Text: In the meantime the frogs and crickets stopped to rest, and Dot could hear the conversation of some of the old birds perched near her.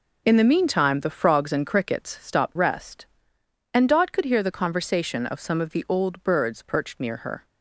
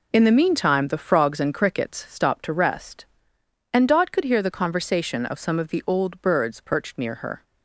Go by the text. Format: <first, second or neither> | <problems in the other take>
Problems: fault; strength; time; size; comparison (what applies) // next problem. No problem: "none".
second | skips "to"; at 2.5 s